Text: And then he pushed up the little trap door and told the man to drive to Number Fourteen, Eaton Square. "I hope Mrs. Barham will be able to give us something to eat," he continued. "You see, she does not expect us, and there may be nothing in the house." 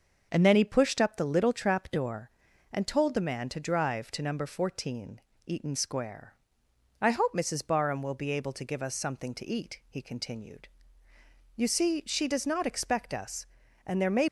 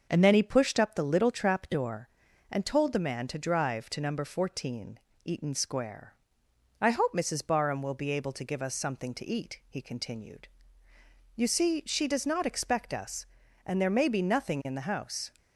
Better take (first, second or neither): second